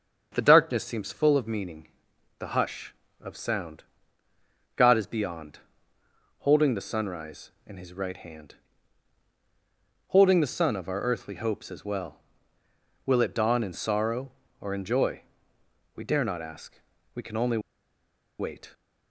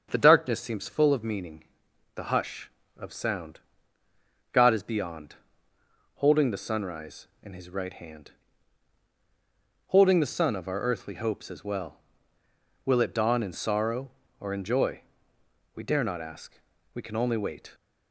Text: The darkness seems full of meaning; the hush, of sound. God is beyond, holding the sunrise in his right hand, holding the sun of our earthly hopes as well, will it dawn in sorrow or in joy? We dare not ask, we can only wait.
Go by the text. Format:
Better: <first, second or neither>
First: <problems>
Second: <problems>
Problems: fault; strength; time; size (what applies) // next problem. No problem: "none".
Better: second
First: starts louder than the rest; strong; until 1.3 s; 7 dB // pauses between "only" and "wait"; noticeable; at 17.5 s; 0.80 s long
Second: starts louder than the rest; strong; until 1.1 s; 7 dB